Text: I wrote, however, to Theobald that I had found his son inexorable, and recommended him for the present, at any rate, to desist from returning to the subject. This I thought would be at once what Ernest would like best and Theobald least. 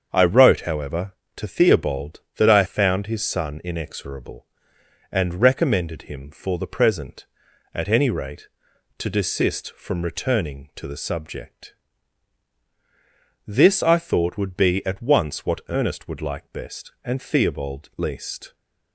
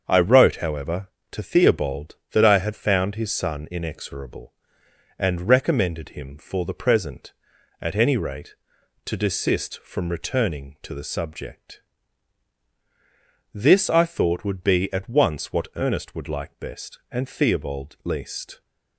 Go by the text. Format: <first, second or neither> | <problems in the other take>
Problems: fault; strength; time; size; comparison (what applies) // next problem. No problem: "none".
second | starts louder than the rest; strong; until 1.1 s; 7 dB; also in the second // skips "had"; at 2.6 s